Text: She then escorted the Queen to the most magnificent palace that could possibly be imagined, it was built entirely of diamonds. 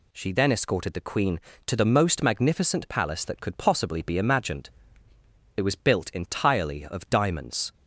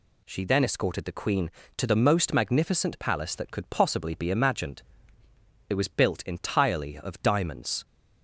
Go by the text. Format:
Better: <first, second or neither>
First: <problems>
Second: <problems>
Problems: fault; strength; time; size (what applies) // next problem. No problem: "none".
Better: neither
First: none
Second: none